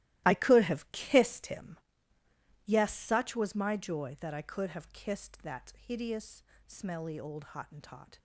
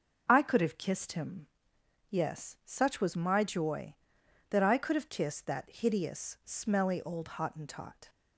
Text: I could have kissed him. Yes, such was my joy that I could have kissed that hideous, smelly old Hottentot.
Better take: second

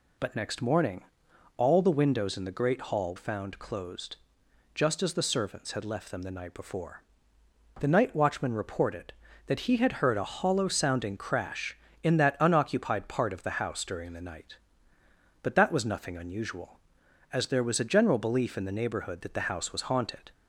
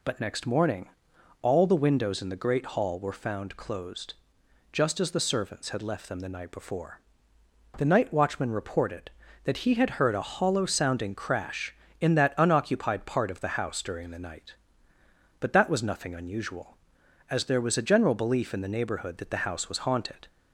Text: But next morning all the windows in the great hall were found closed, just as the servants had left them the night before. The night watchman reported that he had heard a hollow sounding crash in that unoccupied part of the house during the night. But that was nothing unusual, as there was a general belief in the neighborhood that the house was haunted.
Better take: second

